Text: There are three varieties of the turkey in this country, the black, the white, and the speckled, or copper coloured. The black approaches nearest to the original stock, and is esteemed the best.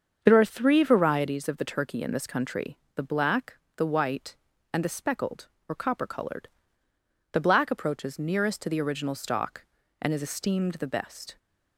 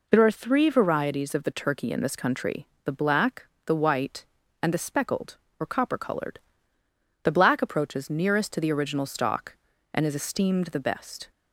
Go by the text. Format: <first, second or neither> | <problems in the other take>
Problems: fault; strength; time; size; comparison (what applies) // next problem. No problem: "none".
second | starts louder than the rest; until 1.4 s; 7 dB